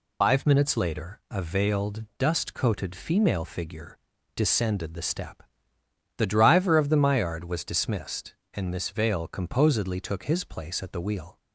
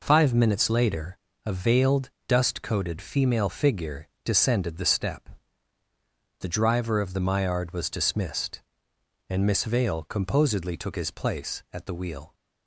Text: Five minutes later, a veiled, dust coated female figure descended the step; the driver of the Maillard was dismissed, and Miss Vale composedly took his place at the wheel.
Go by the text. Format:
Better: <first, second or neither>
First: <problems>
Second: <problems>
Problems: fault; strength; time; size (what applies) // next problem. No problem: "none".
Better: second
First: loses the start of "Five"; at 0.2 s; 70 ms // pauses between "figure" and "descended"; at 3.9 s; 0.38 s long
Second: pauses between "figure" and "descended"; slight; at 4.0 s; 0.16 s long